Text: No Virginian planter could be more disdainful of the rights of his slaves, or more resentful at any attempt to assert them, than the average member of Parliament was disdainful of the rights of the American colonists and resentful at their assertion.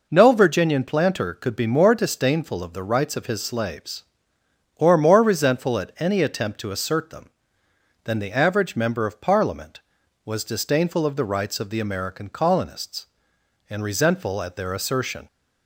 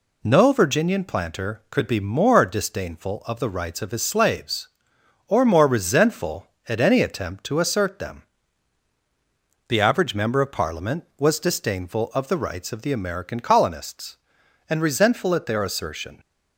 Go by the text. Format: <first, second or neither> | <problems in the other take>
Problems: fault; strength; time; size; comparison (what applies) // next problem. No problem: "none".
first | skips "than"; at 8.9 s